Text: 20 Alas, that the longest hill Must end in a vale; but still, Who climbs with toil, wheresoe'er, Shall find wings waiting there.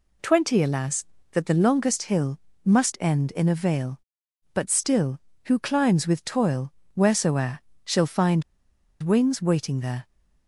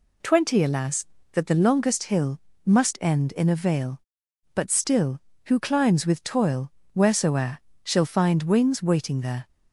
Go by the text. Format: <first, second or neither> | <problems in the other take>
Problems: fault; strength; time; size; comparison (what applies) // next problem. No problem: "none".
second | pauses between "hill" and "Must"; slight; at 2.3 s; 0.26 s long; slight in the second // pauses between "find" and "wings"; noticeable; at 8.4 s; 0.58 s long